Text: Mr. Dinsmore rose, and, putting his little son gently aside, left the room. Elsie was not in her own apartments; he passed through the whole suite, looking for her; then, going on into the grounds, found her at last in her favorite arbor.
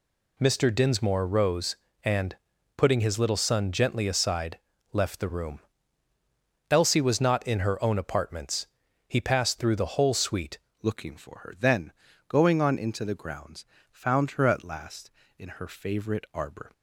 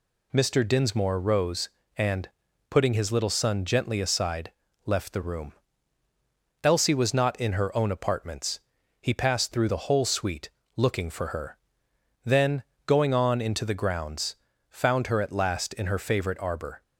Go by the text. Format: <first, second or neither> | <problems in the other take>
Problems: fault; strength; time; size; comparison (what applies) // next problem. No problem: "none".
second | changes voice at "looking"; from 10.8 s on; 5.9 s long